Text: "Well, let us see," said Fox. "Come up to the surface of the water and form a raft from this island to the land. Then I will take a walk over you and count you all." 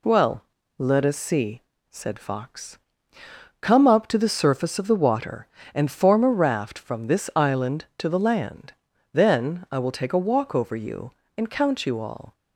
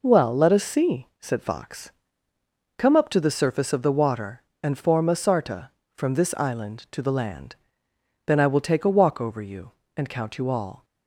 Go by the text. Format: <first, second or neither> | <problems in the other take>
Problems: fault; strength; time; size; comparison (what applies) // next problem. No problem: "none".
first | says "sarta" for "raft"; at 5.1 s